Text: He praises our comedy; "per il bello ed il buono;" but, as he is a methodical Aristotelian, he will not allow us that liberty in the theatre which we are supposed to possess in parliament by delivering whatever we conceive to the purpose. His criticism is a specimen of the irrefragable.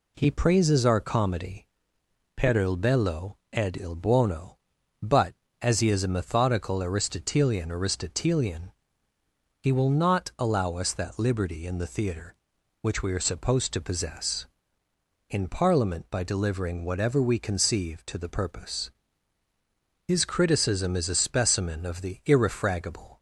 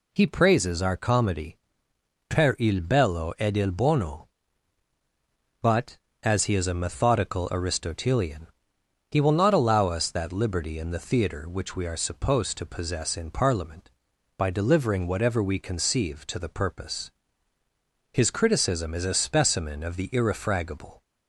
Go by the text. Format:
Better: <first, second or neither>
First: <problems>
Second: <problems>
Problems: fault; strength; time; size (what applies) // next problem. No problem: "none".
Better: second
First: pauses between "bello" and "ed"; slight; at 3.3 s; 0.16 s long // says "Aristotelian" twice; at 7.6 s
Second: none